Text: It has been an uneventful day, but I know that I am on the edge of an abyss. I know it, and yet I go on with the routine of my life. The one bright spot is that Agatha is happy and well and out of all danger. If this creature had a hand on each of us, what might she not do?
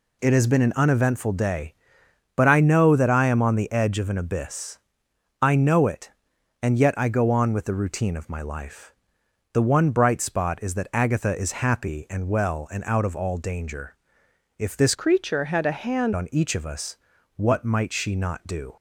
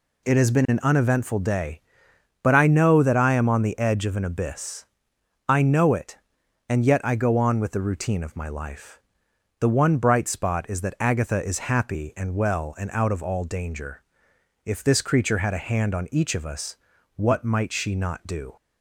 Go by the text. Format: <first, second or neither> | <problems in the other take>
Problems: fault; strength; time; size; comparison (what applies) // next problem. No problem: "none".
second | changes voice from "creature" to "hand"; from 14.9 to 16.1 s; 1.2 s long